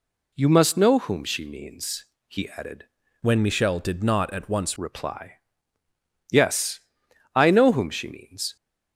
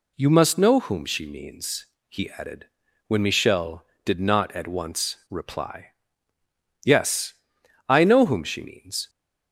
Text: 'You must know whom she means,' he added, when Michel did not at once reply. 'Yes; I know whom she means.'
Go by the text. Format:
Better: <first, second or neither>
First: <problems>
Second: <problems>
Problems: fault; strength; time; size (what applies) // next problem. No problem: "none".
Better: second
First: changes voice from "when" to "once"; from 3.2 to 4.7 s; 1.5 s long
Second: none